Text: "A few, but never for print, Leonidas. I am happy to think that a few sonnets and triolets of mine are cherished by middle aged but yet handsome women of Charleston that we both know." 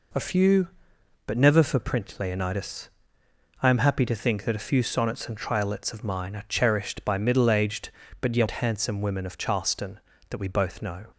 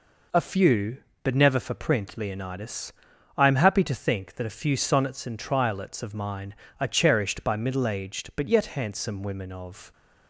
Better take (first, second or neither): first